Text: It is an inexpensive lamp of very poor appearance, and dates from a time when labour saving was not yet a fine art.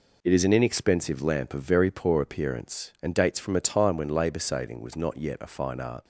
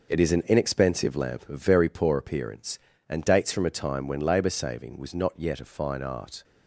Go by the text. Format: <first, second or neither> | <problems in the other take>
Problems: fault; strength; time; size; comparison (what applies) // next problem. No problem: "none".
neither | none